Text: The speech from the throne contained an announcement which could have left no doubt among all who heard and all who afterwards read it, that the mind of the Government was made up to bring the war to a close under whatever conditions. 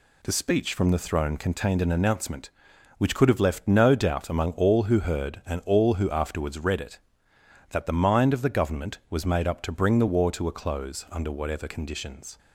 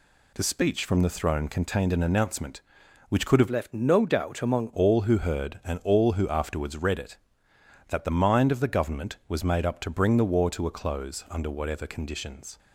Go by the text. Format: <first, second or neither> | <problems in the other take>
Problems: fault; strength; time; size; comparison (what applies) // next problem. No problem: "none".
first | changes voice from "left" to "among"; from 3.4 to 4.7 s; 1.3 s long